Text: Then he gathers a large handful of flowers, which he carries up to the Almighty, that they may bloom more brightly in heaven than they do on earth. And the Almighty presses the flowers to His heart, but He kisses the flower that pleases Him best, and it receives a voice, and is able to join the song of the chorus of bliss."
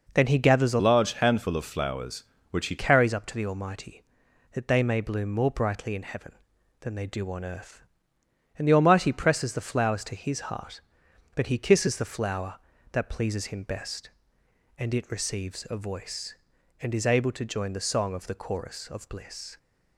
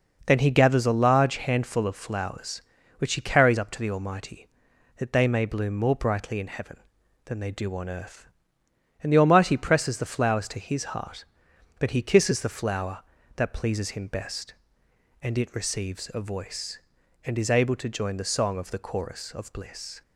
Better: second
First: changes voice from "large" to "he"; from 0.7 to 2.7 s; 2.0 s long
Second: none

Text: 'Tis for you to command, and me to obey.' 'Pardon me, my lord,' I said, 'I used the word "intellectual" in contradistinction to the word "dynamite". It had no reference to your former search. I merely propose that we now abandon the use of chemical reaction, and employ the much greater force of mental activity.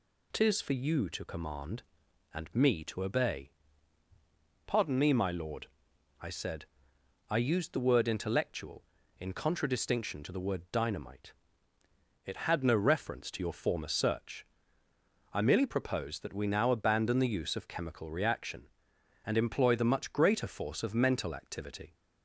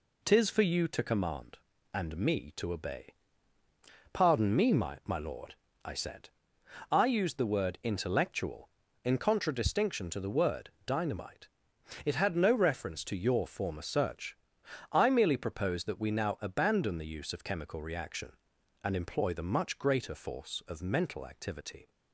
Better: first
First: none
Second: says "my" twice; at 5.0 s // pauses between "word" and "dynamite"; slight; at 10.6 s; 0.16 s long

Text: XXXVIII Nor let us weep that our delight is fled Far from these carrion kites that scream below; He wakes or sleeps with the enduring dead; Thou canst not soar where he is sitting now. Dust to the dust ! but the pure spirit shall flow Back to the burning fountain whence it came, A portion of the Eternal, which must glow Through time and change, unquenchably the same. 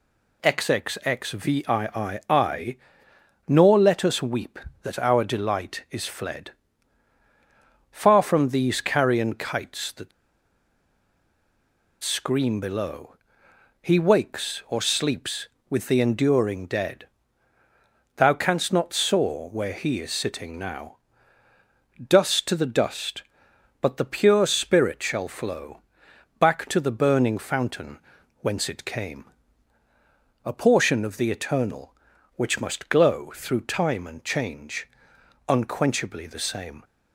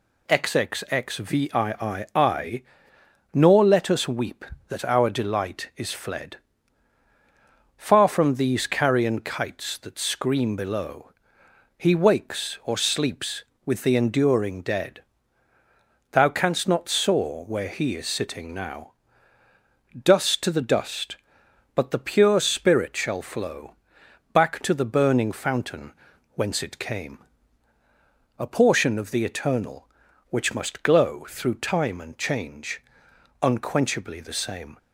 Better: second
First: pauses between "XXXVIII" and "Nor"; strong; at 2.1 s; 1.2 s long // pauses between "fled" and "Far"; strong; at 6.4 s; 1.4 s long // pauses between "that" and "scream"; strong; at 10.1 s; 1.9 s long // pauses between "flow" and "Back"; noticeable; at 25.7 s; 0.58 s long // pauses between "fountain" and "whence"; at 27.9 s; 0.44 s long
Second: pauses between "XXXVIII" and "Nor"; strong; at 2.0 s; 1.2 s long // pauses between "fled" and "Far"; strong; at 6.3 s; 1.4 s long // pauses between "flow" and "Back"; noticeable; at 23.7 s; 0.58 s long // pauses between "fountain" and "whence"; at 25.9 s; 0.44 s long

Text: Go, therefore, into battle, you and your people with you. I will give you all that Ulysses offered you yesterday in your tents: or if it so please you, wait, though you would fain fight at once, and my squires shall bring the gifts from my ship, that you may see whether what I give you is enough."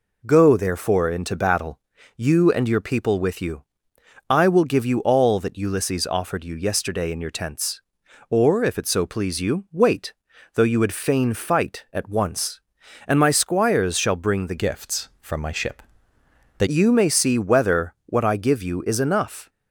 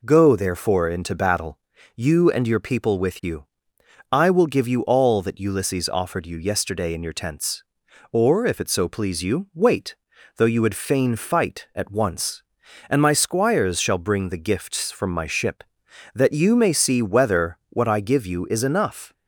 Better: second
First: changes voice from "gifts" to "that"; from 14.5 to 16.6 s; 2.1 s long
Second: none

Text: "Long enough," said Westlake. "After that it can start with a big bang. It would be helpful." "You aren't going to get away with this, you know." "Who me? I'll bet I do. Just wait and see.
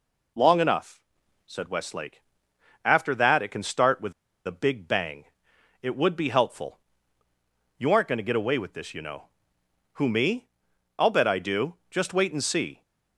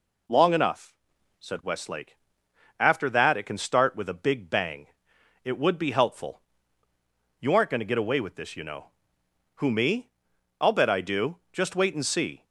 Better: second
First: pauses between "with" and "a"; slight; at 4.1 s; 0.35 s long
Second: none

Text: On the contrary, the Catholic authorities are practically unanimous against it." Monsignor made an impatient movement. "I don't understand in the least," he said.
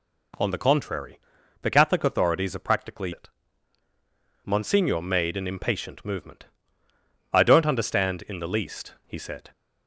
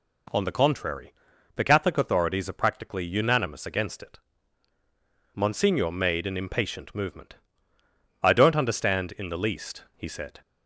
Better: second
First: skips "unanimous against"; at 3.1 s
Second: none

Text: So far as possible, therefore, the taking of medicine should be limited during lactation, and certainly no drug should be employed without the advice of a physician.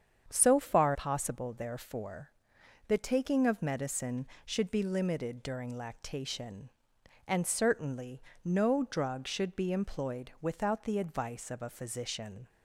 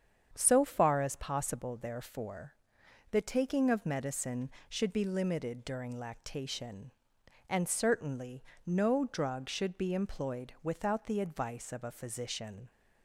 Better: second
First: starts louder than the rest; strong; until 1.2 s; 7.5 dB // skips "as"; at 0.9 s // pauses between "certainly" and "no"; slight; at 8.2 s; 0.20 s long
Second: starts louder than the rest; strong; until 1.3 s; 7.5 dB // pauses between "certainly" and "no"; slight; at 8.4 s; 0.20 s long

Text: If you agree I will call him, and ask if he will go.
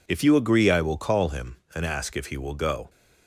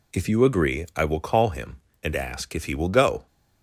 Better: neither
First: none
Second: none

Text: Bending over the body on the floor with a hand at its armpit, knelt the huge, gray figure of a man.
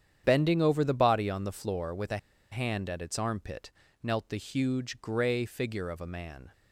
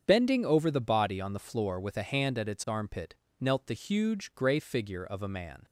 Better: second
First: starts louder than the rest; strong; until 1.2 s; 9 dB // pauses between "a" and "hand"; slight; at 2.1 s; 0.34 s long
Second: starts louder than the rest; strong; until 1.0 s; 7.5 dB

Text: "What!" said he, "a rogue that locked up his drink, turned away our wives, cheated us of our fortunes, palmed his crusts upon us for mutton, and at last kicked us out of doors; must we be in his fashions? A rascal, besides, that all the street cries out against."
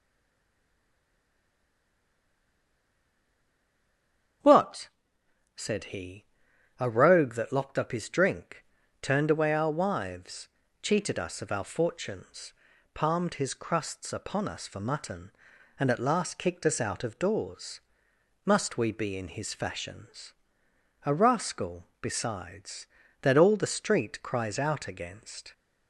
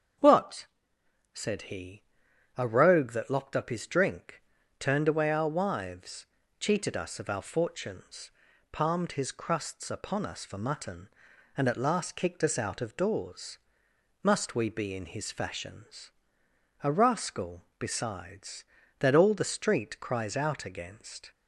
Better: second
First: stays silent before the first word; strong; until 4.4 s; 4.4 s long // starts louder than the rest; strong; until 6.0 s; 7 dB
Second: starts louder than the rest; strong; until 1.8 s; 7 dB

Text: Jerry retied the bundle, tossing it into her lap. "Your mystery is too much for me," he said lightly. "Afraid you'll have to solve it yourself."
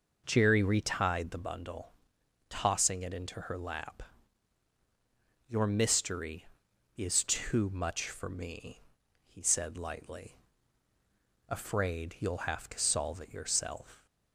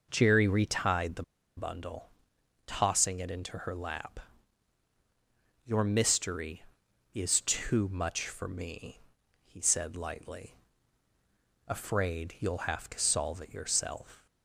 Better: first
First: none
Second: pauses between "the" and "bundle"; slight; at 1.2 s; 0.35 s long

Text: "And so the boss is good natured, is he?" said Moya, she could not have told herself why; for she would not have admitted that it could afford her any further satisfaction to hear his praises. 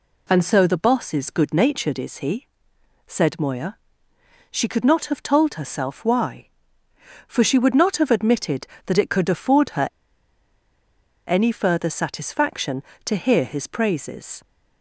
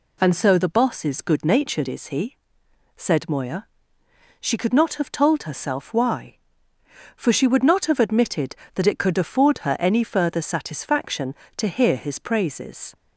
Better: second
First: pauses between "her" and "any"; strong; at 9.8 s; 1.3 s long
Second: none

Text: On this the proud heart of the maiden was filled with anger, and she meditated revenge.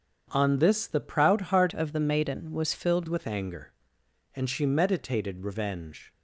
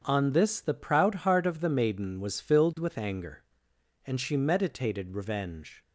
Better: second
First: starts louder than the rest; strong; until 1.3 s; 7 dB // changes voice from "of" to "filled"; from 1.7 to 3.0 s; 1.3 s long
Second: starts louder than the rest; strong; until 1.0 s; 7.5 dB

